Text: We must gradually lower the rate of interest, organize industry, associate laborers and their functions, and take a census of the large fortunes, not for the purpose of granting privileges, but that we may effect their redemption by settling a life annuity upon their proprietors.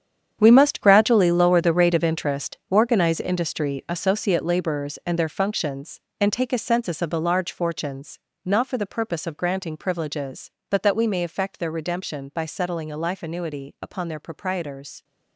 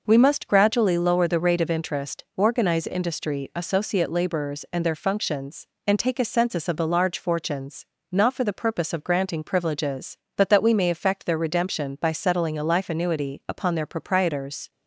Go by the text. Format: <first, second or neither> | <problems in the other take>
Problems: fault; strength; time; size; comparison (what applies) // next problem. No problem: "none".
second | gets quieter; strong; throughout; 13.5 dB